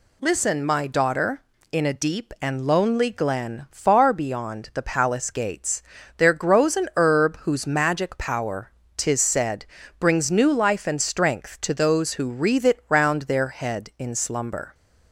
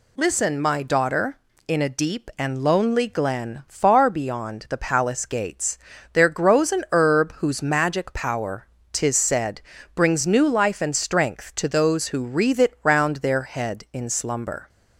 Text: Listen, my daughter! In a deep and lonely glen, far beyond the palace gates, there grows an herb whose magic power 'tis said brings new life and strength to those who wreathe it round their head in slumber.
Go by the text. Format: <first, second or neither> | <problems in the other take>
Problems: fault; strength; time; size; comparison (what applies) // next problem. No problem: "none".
neither | pauses between "power" and "tis"; slight; the same in both // pauses between "said" and "brings"; slight; the same in both